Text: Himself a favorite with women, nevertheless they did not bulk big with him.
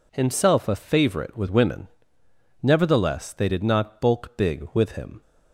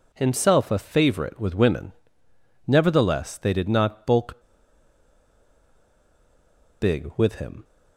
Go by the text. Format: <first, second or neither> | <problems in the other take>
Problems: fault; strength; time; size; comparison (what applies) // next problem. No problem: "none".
first | pauses between "bulk" and "big"; strong; at 4.4 s; 2.3 s long